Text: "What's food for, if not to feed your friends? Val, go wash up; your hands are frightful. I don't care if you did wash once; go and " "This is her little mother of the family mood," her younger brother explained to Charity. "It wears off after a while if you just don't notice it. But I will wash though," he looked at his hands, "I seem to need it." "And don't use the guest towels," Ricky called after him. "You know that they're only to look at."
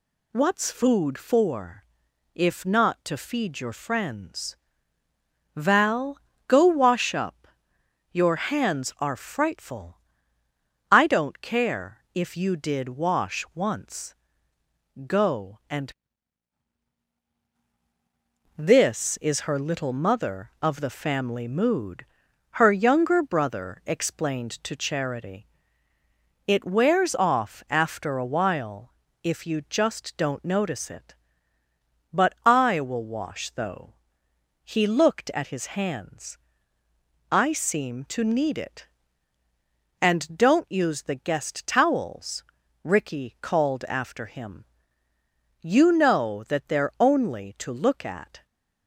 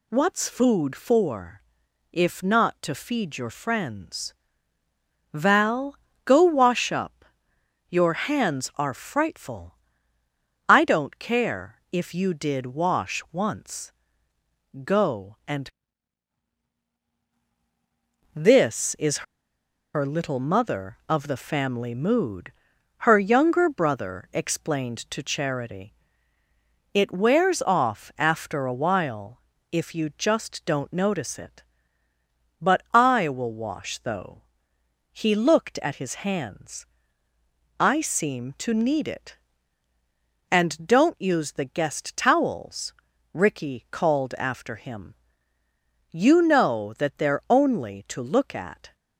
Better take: first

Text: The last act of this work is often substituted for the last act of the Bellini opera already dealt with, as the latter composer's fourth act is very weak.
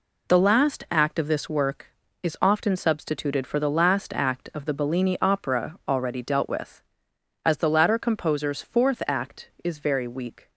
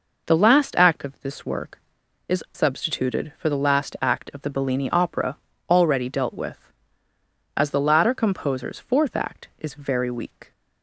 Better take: first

